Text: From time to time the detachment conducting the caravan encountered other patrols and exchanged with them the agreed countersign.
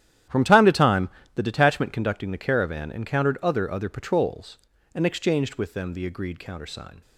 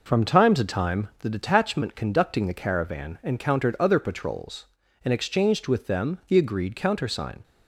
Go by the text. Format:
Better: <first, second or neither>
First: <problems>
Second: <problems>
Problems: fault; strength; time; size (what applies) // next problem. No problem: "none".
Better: second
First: starts louder than the rest; strong; until 1.5 s; 11 dB // pauses between "time" and "the"; slight; at 1.0 s; 0.26 s long // says "other" twice; at 3.7 s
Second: none